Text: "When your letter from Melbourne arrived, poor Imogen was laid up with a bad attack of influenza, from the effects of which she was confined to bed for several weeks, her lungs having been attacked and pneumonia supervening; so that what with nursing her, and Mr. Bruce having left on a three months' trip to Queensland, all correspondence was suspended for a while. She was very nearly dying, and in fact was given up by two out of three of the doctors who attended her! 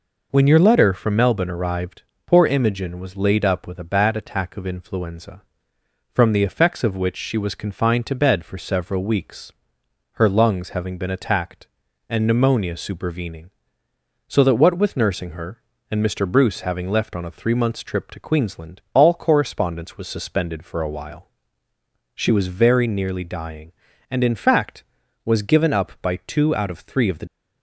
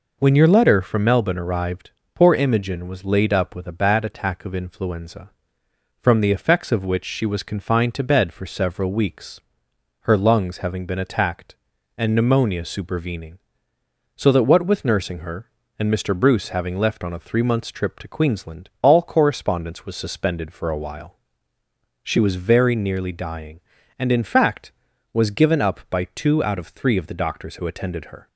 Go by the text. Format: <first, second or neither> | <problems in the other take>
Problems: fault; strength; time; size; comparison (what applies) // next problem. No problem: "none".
second | stops before "doctors who attended her"; at 27.2 s